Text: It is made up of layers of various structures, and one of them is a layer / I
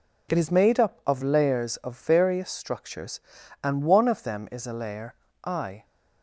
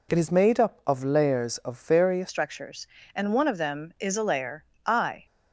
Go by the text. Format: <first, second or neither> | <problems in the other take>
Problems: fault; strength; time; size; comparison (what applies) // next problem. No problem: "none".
first | changes voice at "structures"; from 2.2 s on; 3.0 s long